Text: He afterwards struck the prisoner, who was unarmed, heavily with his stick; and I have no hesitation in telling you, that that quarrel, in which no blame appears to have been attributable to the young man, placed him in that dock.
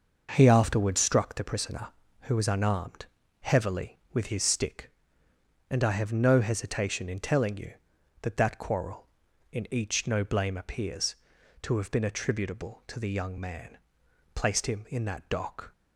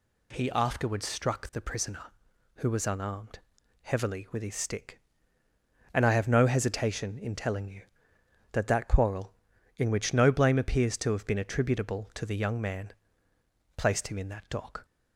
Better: second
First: starts louder than the rest; noticeable; until 1.3 s; 6 dB // says "each" for "which"; at 9.7 s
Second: none

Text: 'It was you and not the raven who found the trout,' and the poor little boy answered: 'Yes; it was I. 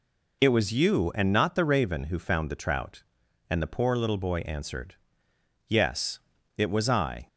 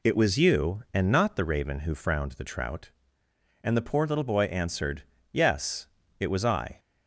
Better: first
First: none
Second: says "frowned" for "found"; at 1.9 s

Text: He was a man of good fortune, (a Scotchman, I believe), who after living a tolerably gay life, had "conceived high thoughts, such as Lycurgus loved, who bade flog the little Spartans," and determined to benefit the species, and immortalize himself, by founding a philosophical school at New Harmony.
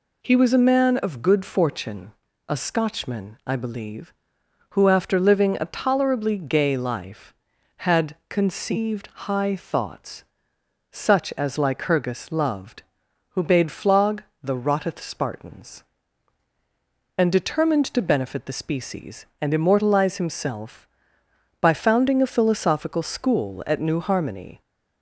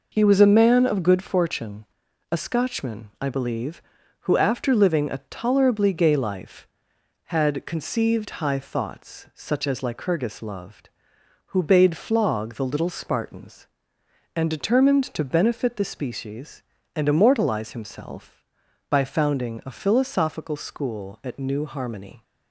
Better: second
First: pauses between "conceived" and "high"; slight; at 9.0 s; 0.16 s long // pauses between "flog" and "the"; slight; at 14.2 s; 0.20 s long // says "rotteth" for "little"; at 14.5 s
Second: none

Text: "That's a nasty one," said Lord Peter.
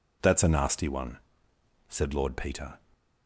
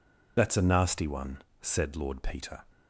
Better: first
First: none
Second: loses the start of "That's"; at 0.3 s; 45 ms

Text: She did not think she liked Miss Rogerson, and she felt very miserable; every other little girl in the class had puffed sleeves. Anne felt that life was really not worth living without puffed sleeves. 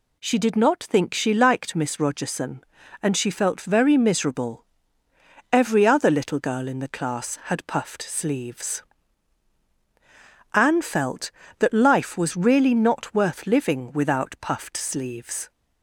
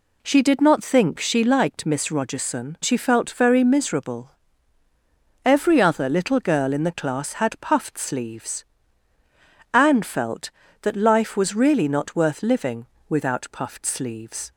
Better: first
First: none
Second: skips "and"; at 2.7 s // pauses between "living" and "without"; slight; at 12.8 s; 0.22 s long

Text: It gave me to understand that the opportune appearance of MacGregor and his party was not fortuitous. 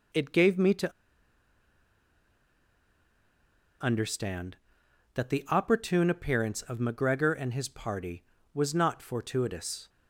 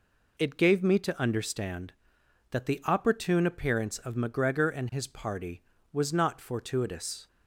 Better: second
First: pauses between "to" and "understand"; strong; at 0.9 s; 2.9 s long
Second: none

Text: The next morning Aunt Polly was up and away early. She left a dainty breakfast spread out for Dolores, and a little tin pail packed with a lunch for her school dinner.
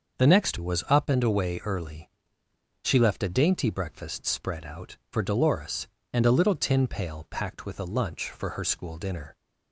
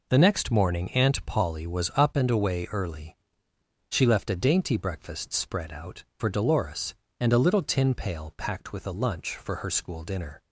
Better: second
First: starts louder than the rest; until 1.2 s; 6 dB // skips "morning Aunt Polly"; at 0.5 s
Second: none

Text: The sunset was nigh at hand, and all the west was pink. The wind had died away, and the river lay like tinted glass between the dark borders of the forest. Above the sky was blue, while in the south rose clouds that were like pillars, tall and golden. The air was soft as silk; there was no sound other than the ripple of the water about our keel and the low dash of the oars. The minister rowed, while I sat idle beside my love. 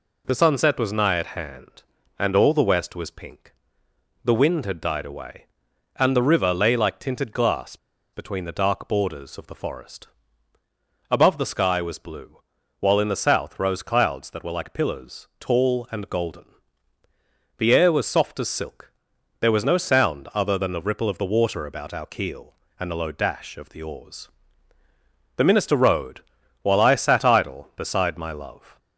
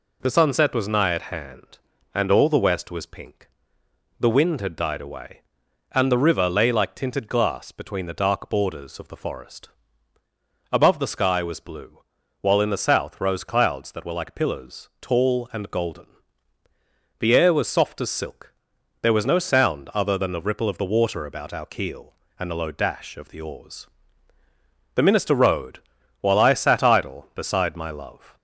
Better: second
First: pauses between "glass" and "between"; at 7.7 s; 0.37 s long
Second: none

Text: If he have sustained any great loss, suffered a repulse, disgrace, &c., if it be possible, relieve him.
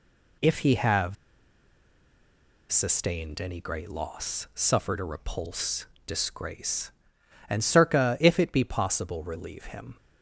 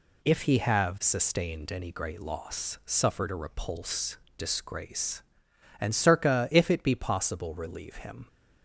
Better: second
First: pauses between "have" and "sustained"; strong; at 1.1 s; 1.5 s long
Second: none

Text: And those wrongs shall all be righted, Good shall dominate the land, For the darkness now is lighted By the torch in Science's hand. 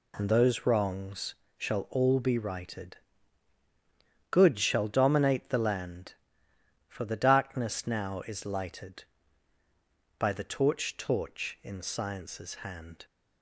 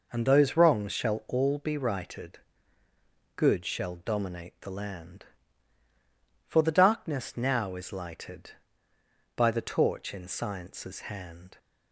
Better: second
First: pauses between "wrongs" and "shall"; slight; at 1.3 s; 0.22 s long // says "torch" twice; at 10.9 s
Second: none

